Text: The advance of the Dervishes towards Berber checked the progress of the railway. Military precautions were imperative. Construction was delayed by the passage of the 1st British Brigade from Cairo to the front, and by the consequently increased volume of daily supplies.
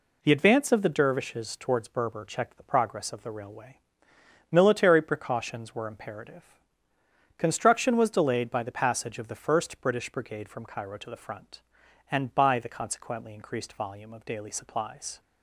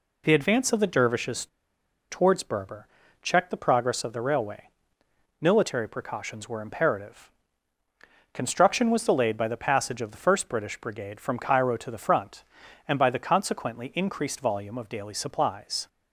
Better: first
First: none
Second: pauses between "Dervishes" and "towards"; noticeable; at 1.4 s; 0.65 s long // pauses between "Berber" and "checked"; at 2.8 s; 0.38 s long

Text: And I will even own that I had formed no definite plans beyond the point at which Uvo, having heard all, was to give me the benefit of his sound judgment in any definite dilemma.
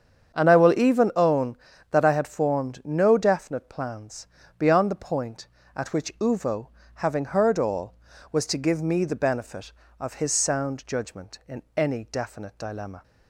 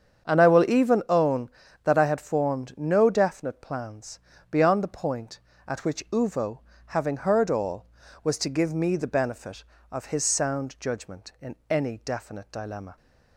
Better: neither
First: starts louder than the rest; strong; until 1.4 s; 7.5 dB // pauses between "plans" and "beyond"; slight; at 4.2 s; 0.32 s long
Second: starts louder than the rest; strong; until 1.3 s; 7.5 dB // pauses between "plans" and "beyond"; slight; at 4.1 s; 0.32 s long

